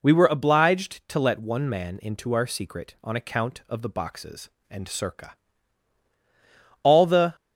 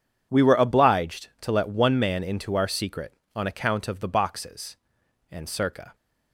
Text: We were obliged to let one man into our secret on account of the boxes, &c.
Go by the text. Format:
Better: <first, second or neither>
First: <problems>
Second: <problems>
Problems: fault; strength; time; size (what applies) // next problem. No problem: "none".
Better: second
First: goes on to say "All the"; from 6.8 s on; 0.52 s long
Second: none